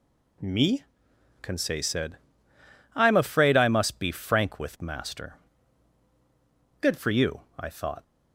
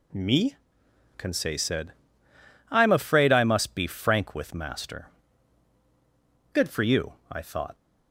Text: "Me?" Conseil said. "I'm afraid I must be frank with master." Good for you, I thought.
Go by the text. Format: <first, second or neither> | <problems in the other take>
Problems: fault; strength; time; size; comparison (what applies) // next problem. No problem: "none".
neither | none